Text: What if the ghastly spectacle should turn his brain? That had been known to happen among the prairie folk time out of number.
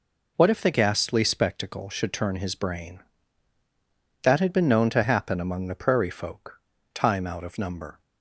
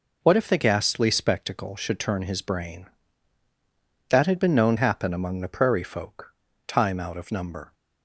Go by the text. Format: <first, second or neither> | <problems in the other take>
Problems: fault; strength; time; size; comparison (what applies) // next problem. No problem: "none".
first | skips "to"; at 4.7 s // pauses between "folk" and "time"; slight; at 6.3 s; 0.34 s long; slight in the first